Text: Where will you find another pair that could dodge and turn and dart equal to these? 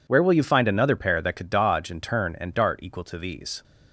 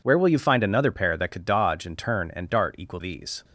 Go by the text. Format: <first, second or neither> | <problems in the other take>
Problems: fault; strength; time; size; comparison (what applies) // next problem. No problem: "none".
first | skips "to"; at 2.9 s